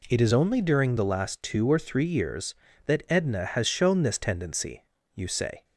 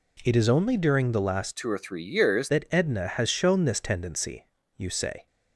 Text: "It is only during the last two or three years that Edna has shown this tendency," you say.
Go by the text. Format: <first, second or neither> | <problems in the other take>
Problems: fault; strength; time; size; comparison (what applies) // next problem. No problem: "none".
first | changes voice from "two" to "years"; from 1.5 to 2.4 s; 0.9 s long